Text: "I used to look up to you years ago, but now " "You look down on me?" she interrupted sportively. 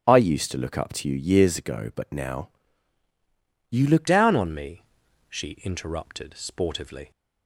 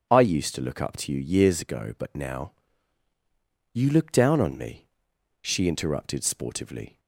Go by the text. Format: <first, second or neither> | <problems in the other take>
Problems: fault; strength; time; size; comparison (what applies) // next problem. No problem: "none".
second | changes voice at "down"; from 4.0 s on; 3.1 s long